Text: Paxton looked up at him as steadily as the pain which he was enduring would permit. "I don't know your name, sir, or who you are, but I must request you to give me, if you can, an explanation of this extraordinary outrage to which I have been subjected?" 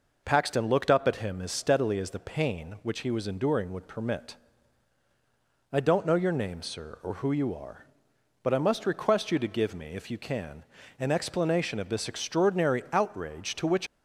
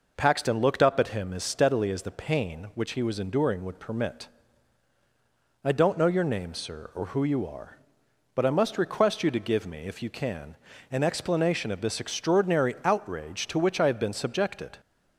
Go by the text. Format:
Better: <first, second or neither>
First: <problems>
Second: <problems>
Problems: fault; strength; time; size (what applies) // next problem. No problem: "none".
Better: second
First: stops before "I have been subjected"; at 13.8 s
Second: none